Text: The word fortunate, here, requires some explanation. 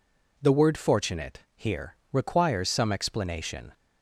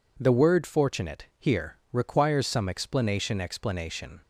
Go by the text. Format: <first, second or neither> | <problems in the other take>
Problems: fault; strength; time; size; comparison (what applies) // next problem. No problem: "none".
first | says "explanation" twice; at 3.3 s